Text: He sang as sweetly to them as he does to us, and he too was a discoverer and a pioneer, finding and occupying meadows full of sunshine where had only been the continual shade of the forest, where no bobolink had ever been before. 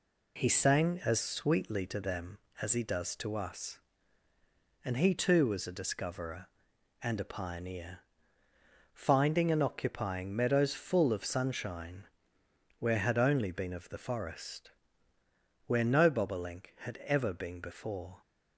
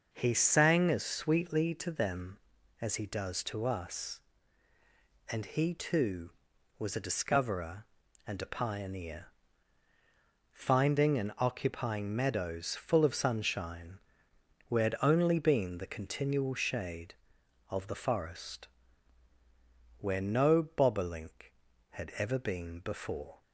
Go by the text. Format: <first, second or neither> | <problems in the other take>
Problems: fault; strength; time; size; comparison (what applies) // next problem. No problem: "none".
second | pauses between "sunshine" and "where"; noticeable; at 12.0 s; 0.74 s long; noticeable in the second // skips "the continual shade"; at 13.7 s